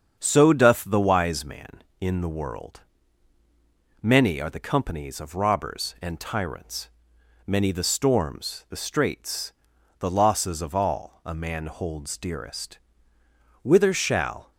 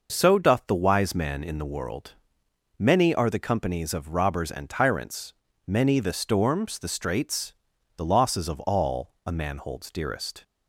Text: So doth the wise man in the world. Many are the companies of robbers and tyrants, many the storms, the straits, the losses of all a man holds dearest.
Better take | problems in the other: second | starts louder than the rest; strong; until 1.2 s; 7.5 dB // goes on to say "Whither shall"; noticeable; from 13.6 s on; 0.90 s long

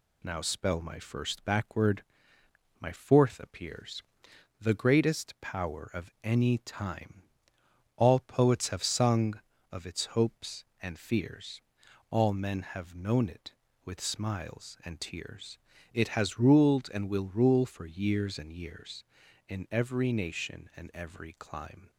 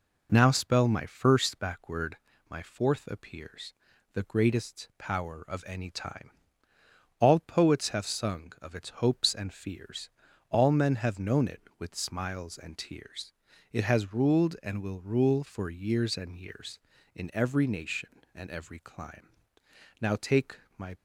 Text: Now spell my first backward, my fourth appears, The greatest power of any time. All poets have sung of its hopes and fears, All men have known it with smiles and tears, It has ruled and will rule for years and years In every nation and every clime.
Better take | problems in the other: first | goes on to say "Now take my"; noticeable; from 20.0 s on; 0.94 s long

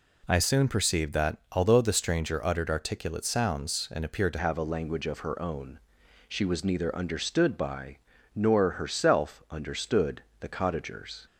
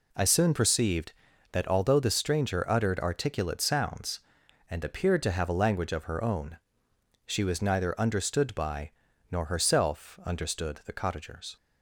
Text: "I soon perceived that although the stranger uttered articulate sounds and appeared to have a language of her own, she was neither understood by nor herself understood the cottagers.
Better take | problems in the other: second | changes voice at "have"; from 4.3 s on; 6.9 s long // pauses between "by" and "nor"; at 7.9 s; 0.38 s long; also in the second // pauses between "understood" and "the"; slight; at 10.2 s; 0.20 s long

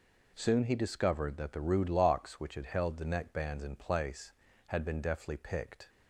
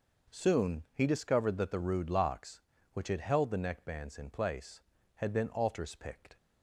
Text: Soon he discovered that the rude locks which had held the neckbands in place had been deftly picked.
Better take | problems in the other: first | says "altars" for "deftly"; at 5.5 s

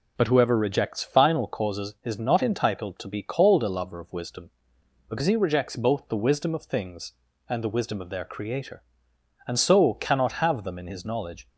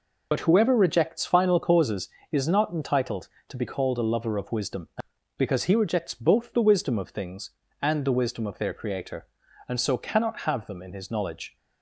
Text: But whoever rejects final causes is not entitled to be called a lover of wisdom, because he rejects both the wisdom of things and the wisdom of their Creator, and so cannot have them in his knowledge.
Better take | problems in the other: first | loses the start of "But"; at 0.3 s; 40 ms

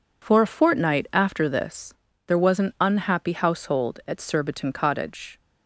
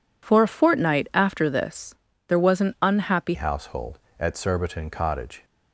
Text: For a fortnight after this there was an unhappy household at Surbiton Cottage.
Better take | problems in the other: first | pauses between "this" and "there"; slight; at 1.9 s; 0.34 s long; slight in the first // changes voice at "household"; from 3.3 s on; 2.1 s long

